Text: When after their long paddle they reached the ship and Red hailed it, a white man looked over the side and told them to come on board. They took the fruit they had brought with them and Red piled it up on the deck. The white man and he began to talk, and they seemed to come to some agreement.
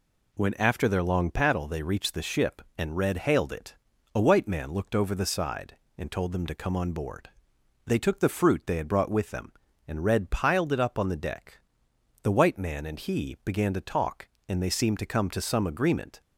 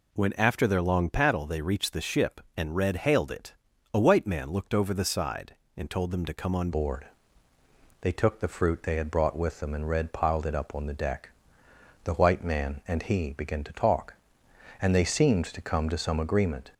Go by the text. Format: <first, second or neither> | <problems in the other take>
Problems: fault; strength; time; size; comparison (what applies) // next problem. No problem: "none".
first | changes voice at "board"; from 6.7 s on; 10.0 s long